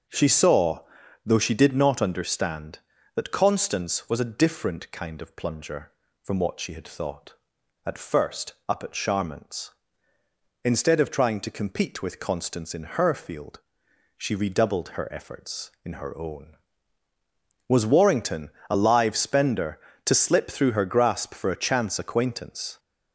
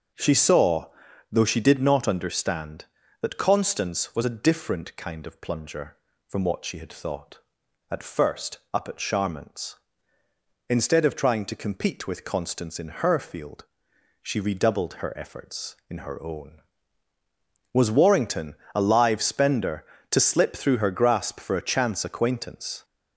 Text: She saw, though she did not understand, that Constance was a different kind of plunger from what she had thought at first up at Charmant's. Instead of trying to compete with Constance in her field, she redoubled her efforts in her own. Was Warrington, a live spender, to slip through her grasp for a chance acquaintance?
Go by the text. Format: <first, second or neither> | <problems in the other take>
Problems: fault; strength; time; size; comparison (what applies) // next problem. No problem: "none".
neither | starts louder than the rest; the same in both // pauses between "first" and "up"; slight; the same in both